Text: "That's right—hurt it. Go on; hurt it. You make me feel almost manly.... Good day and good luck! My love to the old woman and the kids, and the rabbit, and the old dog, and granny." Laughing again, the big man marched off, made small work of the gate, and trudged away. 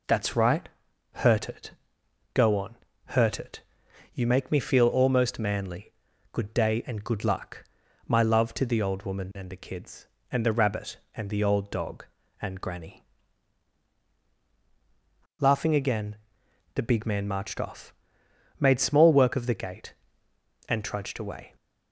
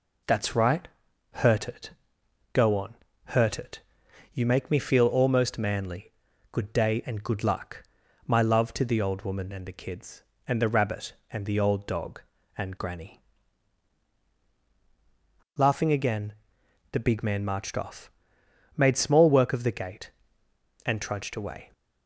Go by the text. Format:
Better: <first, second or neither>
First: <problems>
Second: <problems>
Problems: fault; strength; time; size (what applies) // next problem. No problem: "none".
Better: neither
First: none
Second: none